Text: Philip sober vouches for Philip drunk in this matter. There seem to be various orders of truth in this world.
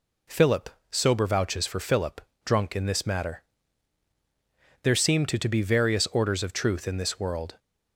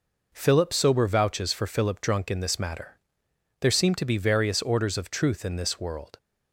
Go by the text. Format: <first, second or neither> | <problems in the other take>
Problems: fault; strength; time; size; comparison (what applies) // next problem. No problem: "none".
second | pauses between "Philip" and "sober"; slight; at 0.6 s; 0.22 s long // pauses between "Philip" and "drunk"; slight; at 2.2 s; 0.24 s long // says "to" twice; at 5.3 s